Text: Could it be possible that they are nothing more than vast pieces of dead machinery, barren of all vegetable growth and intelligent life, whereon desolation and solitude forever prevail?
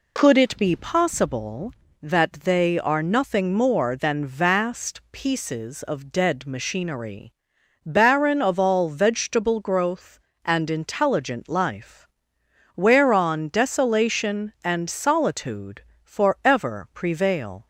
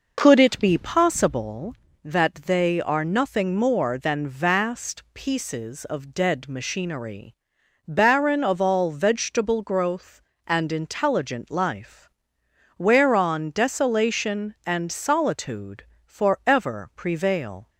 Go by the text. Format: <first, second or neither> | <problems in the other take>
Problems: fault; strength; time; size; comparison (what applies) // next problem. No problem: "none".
first | starts louder than the rest; noticeable; until 1.6 s; 5.5 dB // pauses between "solitude" and "forever"; slight; at 15.8 s; 0.20 s long; slight in the first